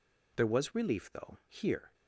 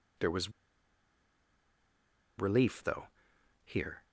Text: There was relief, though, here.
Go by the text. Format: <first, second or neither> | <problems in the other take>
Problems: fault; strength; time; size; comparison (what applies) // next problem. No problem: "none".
first | pauses between "was" and "relief"; strong; at 0.5 s; 1.8 s long